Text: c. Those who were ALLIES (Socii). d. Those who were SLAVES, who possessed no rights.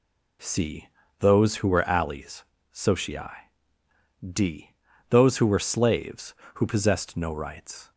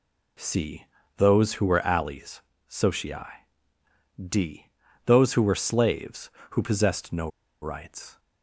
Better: first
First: none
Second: pauses between "no" and "rights"; slight; at 7.2 s; 0.34 s long

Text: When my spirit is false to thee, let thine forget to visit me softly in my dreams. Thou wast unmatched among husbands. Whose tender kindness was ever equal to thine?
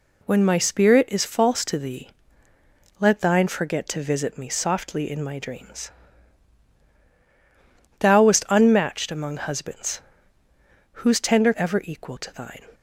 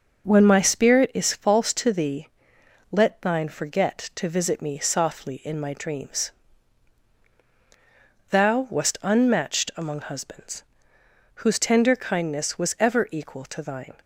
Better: second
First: skips "kindness was"; at 11.5 s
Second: none

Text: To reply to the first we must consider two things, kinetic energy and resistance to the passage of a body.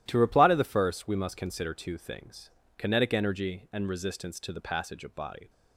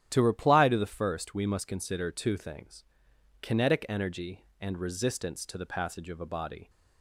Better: second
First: starts louder than the rest; strong; until 1.0 s; 12.5 dB // skips "a"; at 5.1 s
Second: starts louder than the rest; strong; until 1.1 s; 10.5 dB

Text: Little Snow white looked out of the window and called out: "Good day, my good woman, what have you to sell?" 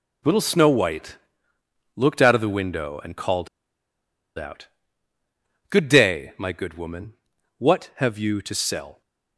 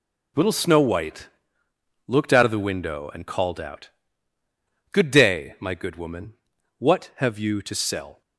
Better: second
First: pauses between "white" and "looked"; noticeable; at 1.1 s; 0.80 s long // pauses between "called" and "out"; noticeable; at 3.4 s; 0.90 s long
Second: pauses between "white" and "looked"; noticeable; at 1.2 s; 0.80 s long

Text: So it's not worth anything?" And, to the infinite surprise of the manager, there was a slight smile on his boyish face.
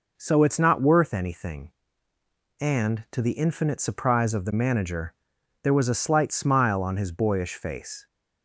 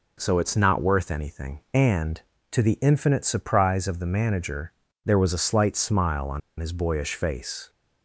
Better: first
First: none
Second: pauses between "on" and "his"; slight; at 6.4 s; 0.19 s long

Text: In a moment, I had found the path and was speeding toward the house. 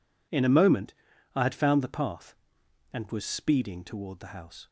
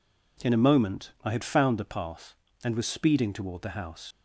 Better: first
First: none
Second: leaves "house" unfinished; at 4.1 s; 75 ms

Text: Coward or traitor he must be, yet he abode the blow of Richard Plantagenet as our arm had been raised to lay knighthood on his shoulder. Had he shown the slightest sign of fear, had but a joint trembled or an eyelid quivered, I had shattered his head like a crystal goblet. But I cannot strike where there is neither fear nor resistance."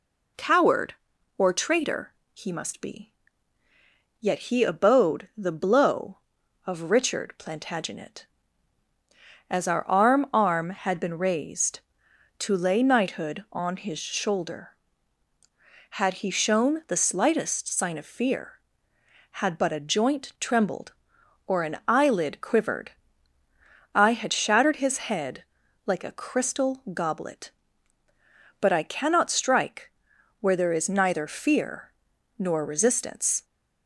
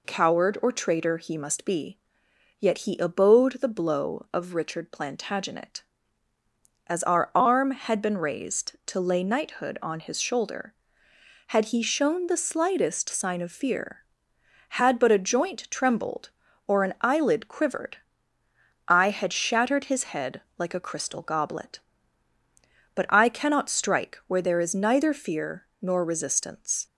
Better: second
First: pauses between "traitor" and "he"; slight; at 2.1 s; 0.20 s long // says "arm" twice; at 10.3 s // pauses between "head" and "like"; at 25.4 s; 0.42 s long // pauses between "strike" and "where"; noticeable; at 29.9 s; 0.50 s long // pauses between "fear" and "nor"; noticeable; at 31.9 s; 0.46 s long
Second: pauses between "head" and "like"; slight; at 20.4 s; 0.18 s long // pauses between "fear" and "nor"; slight; at 25.6 s; 0.16 s long

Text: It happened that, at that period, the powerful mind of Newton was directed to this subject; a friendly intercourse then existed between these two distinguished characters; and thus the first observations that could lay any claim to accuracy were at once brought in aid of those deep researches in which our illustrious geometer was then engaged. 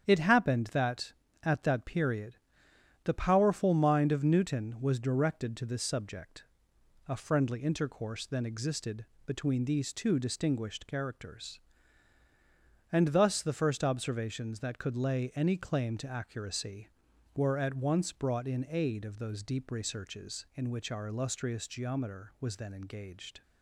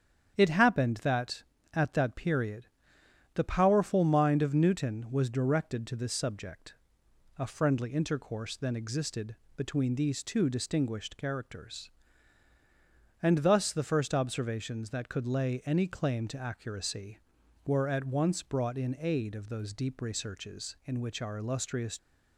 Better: first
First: starts louder than the rest; strong; until 1.0 s; 8.5 dB // pauses between "existed" and "between"; slight; at 9.0 s; 0.22 s long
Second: starts louder than the rest; strong; until 1.3 s; 8.5 dB // pauses between "existed" and "between"; slight; at 9.3 s; 0.22 s long // stops before "geometer was then engaged"; at 21.9 s

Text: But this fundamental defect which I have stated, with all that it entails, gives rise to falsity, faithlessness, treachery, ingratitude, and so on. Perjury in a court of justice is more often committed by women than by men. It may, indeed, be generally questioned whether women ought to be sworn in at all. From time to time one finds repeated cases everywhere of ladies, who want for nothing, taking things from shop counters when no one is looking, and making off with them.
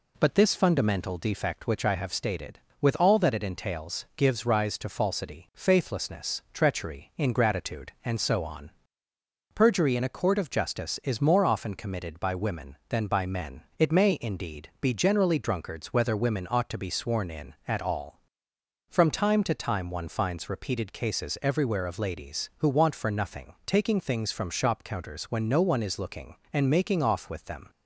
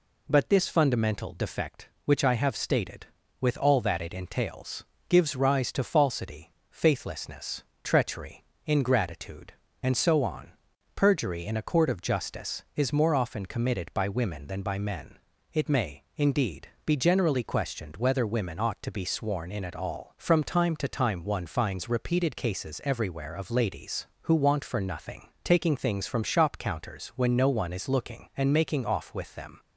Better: second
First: says "drunkards" for "questioned"; at 15.3 s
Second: none

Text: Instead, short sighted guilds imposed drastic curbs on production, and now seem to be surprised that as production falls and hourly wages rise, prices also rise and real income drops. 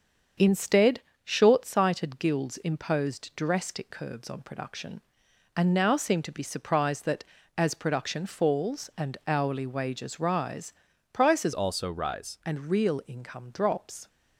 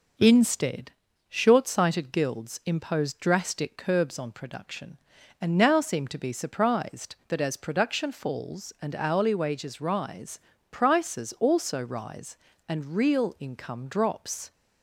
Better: second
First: starts louder than the rest; until 1.6 s; 7 dB // changes voice from "also" to "rise"; from 11.5 to 12.3 s; 0.8 s long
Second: none

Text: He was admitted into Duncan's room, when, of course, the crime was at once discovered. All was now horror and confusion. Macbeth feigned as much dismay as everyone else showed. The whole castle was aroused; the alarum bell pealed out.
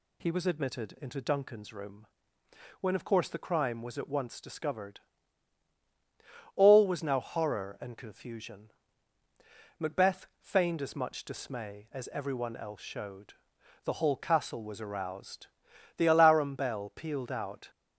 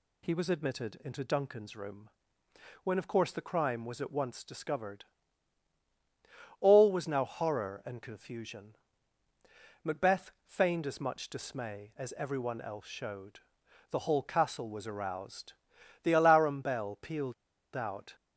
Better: first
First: none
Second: pauses between "pealed" and "out"; at 17.3 s; 0.40 s long

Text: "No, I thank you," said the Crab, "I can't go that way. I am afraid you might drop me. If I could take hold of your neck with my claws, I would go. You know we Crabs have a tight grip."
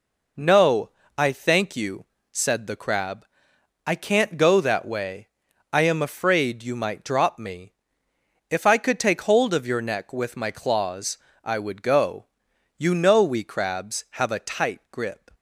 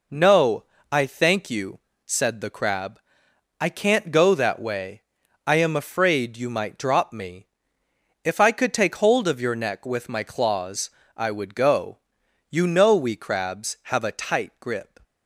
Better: neither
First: none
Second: none

